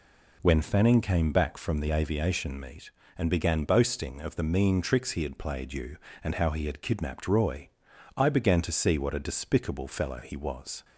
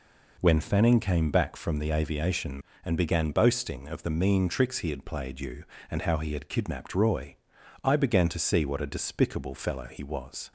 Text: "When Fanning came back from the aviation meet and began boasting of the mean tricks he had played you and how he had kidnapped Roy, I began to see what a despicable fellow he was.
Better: first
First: none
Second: skips "meet"; at 2.7 s

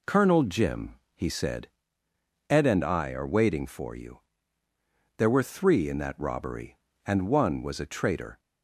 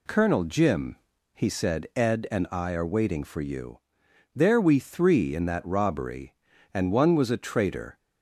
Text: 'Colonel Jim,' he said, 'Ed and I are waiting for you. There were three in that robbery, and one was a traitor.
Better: first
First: none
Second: says "we" for "were"; at 4.6 s

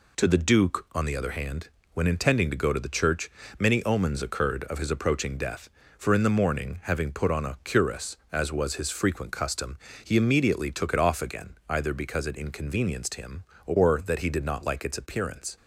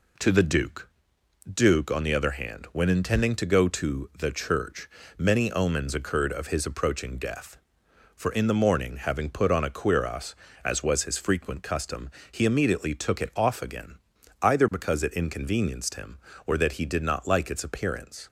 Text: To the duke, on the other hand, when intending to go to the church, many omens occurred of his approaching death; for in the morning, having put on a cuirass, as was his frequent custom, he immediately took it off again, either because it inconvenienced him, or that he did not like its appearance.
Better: first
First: none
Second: says "duke" twice; at 1.5 s

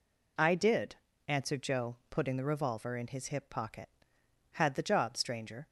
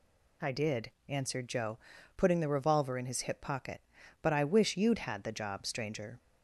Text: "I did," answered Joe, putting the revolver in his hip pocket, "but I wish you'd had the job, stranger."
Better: second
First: skips "but I wish you'd"; at 4.2 s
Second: none

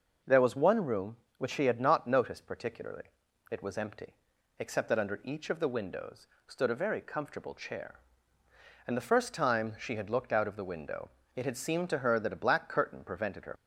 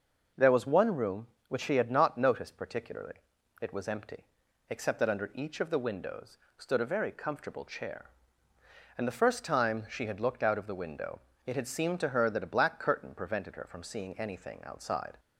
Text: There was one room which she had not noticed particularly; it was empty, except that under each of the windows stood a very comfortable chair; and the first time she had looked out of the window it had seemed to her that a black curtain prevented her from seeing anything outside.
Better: second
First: pauses between "windows" and "stood"; slight; at 6.2 s; 0.18 s long // pauses between "window" and "it"; slight; at 11.1 s; 0.24 s long // stops before "from seeing anything outside"; at 13.5 s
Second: pauses between "windows" and "stood"; slight; at 6.3 s; 0.18 s long // pauses between "window" and "it"; slight; at 11.2 s; 0.24 s long

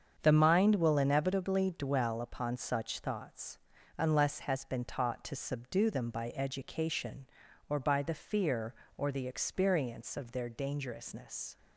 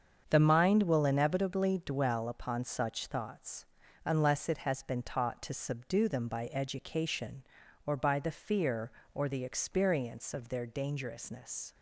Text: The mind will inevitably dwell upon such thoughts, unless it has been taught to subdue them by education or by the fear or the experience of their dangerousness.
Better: second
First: starts louder than the rest; strong; until 1.2 s; 7.5 dB // skips "it"; at 4.4 s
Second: starts louder than the rest; strong; until 1.3 s; 7 dB

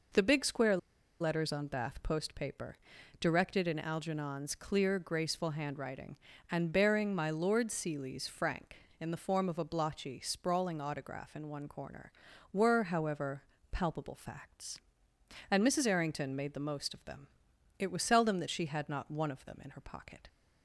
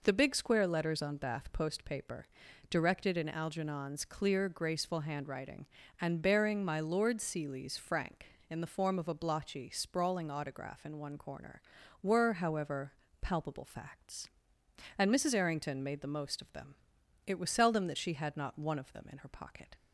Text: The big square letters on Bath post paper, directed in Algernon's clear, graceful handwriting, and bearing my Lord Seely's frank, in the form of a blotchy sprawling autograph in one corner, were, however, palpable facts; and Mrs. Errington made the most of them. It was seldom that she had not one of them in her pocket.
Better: second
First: pauses between "square" and "letters"; at 0.7 s; 0.43 s long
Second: none

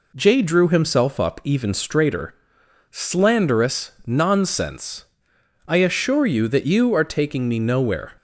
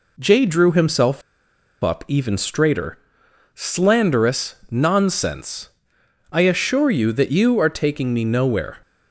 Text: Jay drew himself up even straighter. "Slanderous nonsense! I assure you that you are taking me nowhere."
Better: first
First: pauses between "Slanderous" and "nonsense"; slight; at 3.9 s; 0.15 s long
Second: pauses between "himself" and "up"; noticeable; at 1.2 s; 0.61 s long // pauses between "Slanderous" and "nonsense"; slight; at 4.5 s; 0.16 s long

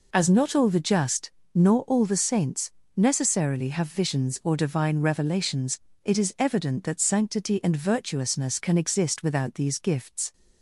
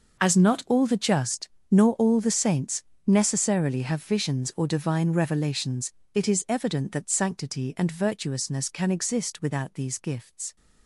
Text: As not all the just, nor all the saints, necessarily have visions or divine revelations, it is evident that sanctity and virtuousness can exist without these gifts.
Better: first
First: none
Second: gets quieter; strong; throughout; 15 dB

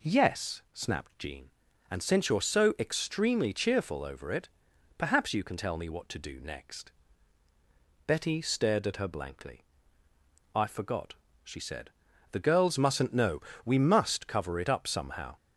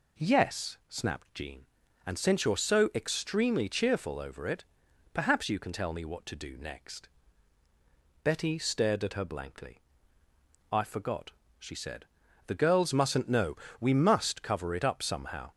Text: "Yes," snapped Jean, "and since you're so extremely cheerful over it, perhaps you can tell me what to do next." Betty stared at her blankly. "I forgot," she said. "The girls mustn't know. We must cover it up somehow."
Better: neither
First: none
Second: none

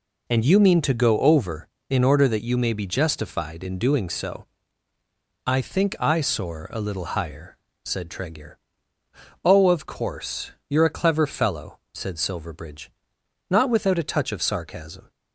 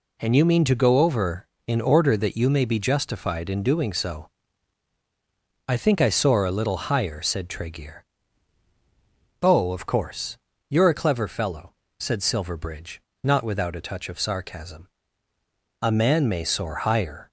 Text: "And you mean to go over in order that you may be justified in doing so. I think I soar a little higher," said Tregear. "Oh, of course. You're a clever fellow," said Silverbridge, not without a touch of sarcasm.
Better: first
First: none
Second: goes on to say "A man may soar higher"; from 15.8 s on; 1.4 s long

